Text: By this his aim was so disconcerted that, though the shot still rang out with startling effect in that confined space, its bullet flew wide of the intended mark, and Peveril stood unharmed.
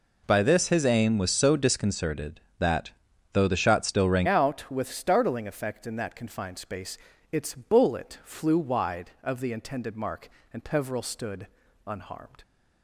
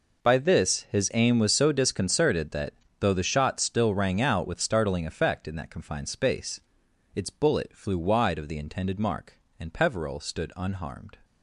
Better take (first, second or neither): second